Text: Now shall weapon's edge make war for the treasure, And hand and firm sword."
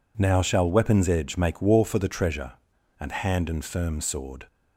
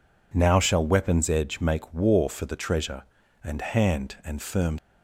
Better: first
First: none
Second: stops before "sword"; at 4.7 s

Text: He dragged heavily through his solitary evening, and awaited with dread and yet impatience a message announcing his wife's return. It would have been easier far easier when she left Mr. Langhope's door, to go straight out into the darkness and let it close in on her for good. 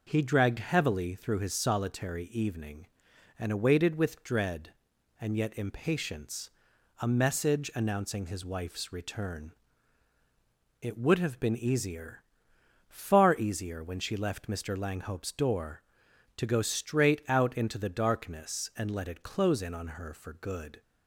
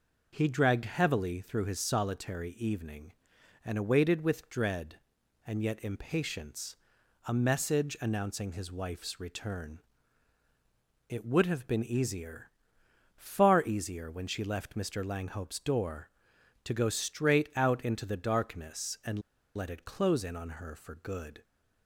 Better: first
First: pauses between "impatience" and "a"; noticeable; at 6.4 s; 0.54 s long // pauses between "easier" and "far"; noticeable; at 12.2 s; 0.66 s long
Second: pauses between "impatience" and "a"; noticeable; at 6.7 s; 0.54 s long // pauses between "easier" and "far"; noticeable; at 12.4 s; 0.66 s long // pauses between "and" and "let"; slight; at 19.2 s; 0.34 s long

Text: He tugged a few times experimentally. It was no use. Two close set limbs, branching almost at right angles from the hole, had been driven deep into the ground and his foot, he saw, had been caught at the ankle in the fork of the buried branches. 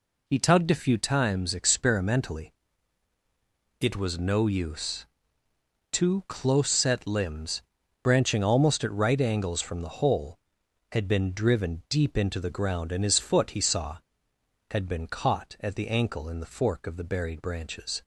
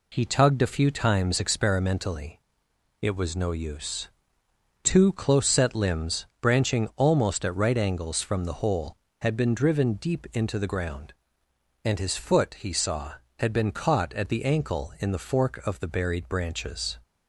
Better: neither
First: none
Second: none

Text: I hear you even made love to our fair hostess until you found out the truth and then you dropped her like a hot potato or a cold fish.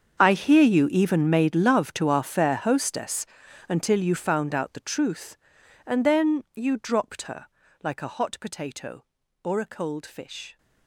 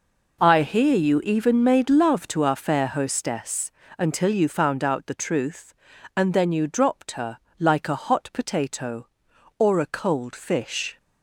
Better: second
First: gets quieter; strong; throughout; 18 dB // pauses between "hostess" and "until"; noticeable; at 3.2 s; 0.46 s long // pauses between "her" and "like"; at 7.4 s; 0.38 s long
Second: pauses between "hostess" and "until"; slight; at 3.7 s; 0.26 s long // pauses between "her" and "like"; slight; at 7.3 s; 0.20 s long

